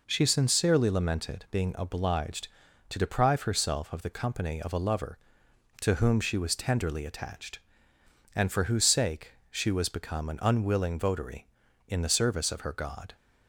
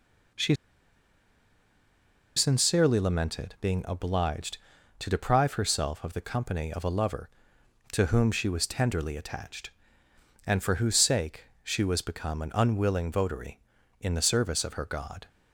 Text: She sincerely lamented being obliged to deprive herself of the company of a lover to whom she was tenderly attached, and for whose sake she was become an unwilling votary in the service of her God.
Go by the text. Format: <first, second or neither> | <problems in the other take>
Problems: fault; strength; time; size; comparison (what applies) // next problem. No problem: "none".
first | pauses between "She" and "sincerely"; strong; at 0.5 s; 1.8 s long // pauses between "sake" and "she"; slight; at 11.4 s; 0.16 s long; slight in the first